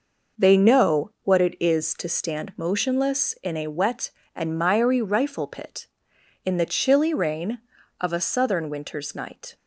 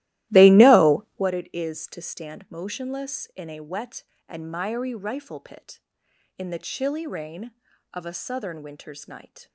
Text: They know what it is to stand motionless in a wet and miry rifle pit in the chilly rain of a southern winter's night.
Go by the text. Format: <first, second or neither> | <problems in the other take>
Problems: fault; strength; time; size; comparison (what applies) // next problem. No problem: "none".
first | starts louder than the rest; strong; until 1.3 s; 16 dB